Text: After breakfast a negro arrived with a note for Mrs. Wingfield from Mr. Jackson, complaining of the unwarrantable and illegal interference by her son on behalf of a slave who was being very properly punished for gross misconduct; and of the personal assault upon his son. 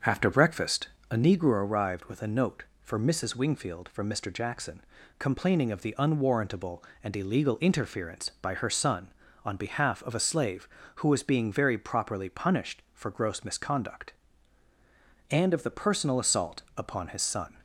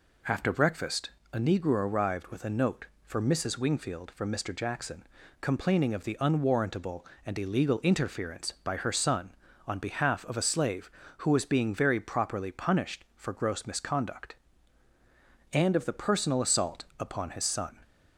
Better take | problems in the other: second | starts louder than the rest; until 1.6 s; 6.5 dB // pauses between "breakfast" and "a"; slight; at 0.8 s; 0.24 s long; slight in the second // pauses between "assault" and "upon"; slight; at 16.6 s; 0.16 s long; slight in the second

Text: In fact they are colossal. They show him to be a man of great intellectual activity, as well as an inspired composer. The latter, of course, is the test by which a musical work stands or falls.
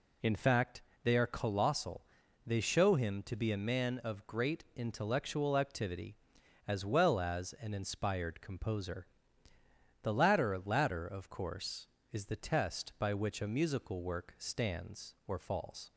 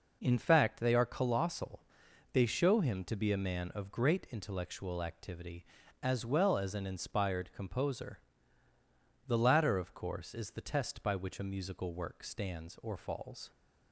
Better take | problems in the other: second | pauses between "fact" and "they"; slight; at 0.8 s; 0.24 s long // says "latter" twice; at 10.6 s

